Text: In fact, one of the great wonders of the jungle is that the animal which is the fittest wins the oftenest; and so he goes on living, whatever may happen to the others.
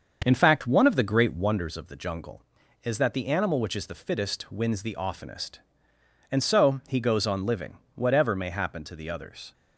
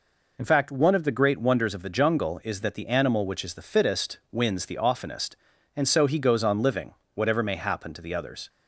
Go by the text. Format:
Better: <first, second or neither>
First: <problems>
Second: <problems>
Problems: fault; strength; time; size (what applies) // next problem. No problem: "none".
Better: second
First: starts louder than the rest; until 1.7 s; 6.5 dB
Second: none